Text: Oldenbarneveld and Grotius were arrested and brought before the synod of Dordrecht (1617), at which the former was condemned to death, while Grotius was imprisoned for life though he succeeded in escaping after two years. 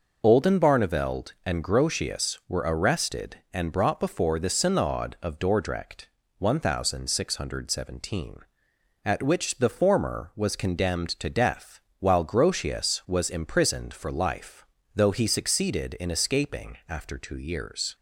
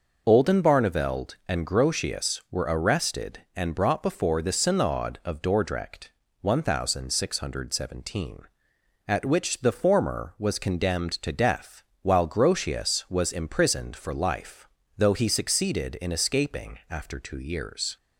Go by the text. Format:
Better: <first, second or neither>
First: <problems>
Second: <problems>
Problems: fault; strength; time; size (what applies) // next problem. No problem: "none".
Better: neither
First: pauses between "life" and "though"; slight; at 14.6 s; 0.28 s long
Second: pauses between "life" and "though"; slight; at 14.6 s; 0.28 s long